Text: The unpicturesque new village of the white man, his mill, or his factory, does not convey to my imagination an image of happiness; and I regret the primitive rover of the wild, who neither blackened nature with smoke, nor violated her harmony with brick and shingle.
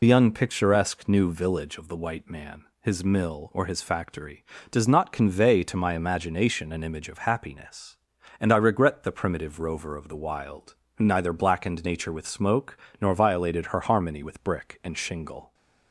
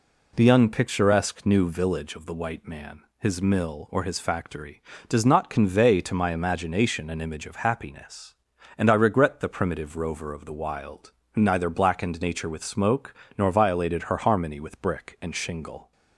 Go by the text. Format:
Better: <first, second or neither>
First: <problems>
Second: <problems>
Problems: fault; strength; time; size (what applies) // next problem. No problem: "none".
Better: second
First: loses the start of "The"; at 0.0 s; 65 ms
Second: none